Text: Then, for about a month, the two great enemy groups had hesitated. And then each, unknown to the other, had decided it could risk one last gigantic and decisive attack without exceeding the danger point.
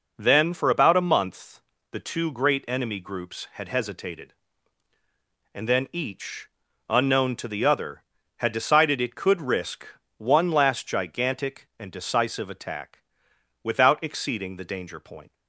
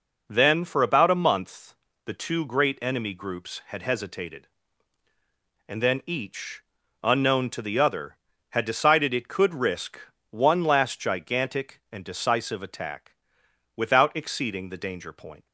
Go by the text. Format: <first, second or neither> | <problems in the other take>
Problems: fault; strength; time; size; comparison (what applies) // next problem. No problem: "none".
neither | pauses between "risk" and "one"; slight; the same in both // pauses between "attack" and "without"; noticeable; the same in both